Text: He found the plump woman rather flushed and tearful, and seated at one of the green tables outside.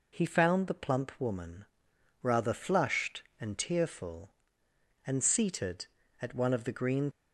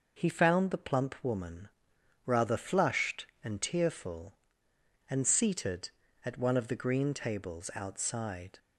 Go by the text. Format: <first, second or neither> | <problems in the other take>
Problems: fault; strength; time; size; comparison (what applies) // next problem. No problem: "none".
second | pauses between "woman" and "rather"; noticeable; at 1.6 s; 0.56 s long; noticeable in the second // stops before "tables outside"; at 7.1 s